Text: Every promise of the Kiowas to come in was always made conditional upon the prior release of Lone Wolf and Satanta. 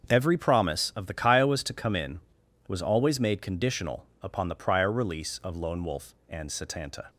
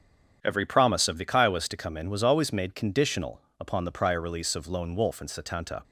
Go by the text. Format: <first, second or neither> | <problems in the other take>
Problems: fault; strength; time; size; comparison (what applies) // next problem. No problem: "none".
neither | starts louder than the rest; the same in both // pauses between "conditional" and "upon"; slight; the same in both